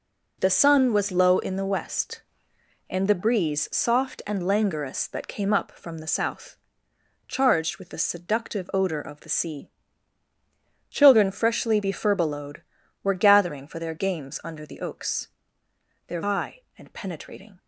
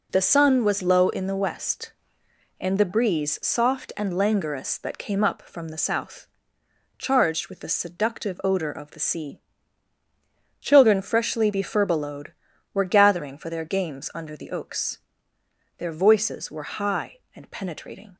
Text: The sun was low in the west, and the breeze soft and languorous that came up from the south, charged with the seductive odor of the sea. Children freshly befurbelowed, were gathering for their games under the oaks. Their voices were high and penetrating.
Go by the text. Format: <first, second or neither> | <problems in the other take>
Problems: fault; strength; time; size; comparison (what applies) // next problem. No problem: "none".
second | skips "voices were"; at 16.2 s